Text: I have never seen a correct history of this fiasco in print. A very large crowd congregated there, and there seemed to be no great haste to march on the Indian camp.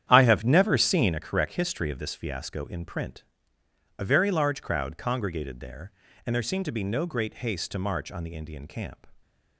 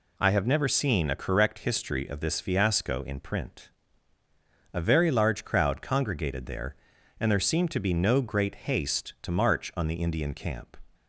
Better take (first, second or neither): second